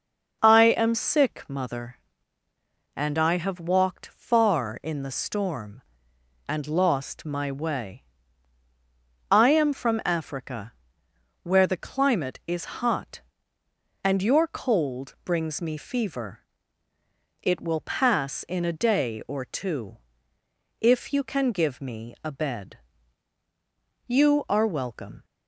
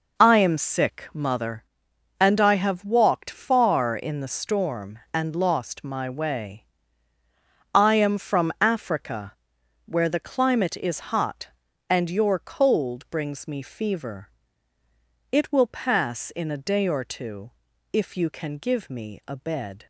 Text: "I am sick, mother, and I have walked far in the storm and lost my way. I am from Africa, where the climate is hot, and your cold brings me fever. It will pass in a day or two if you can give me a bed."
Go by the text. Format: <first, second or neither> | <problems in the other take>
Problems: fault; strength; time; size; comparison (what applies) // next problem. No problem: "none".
second | pauses between "two" and "if"; noticeable; at 19.9 s; 0.82 s long; also in the second // goes on to say "You are welcome"; noticeable; from 24.0 s on; 1.1 s long